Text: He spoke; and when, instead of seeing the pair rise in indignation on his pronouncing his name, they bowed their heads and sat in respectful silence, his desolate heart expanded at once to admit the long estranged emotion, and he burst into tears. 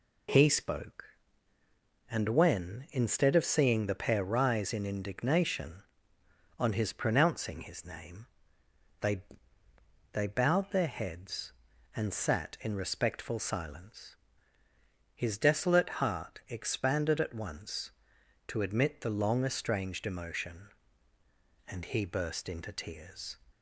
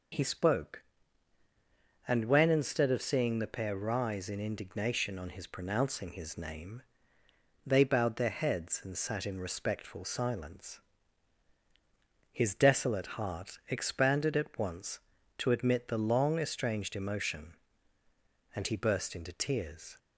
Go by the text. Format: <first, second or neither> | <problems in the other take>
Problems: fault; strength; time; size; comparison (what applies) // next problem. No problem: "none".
second | says "they" twice; at 10.1 s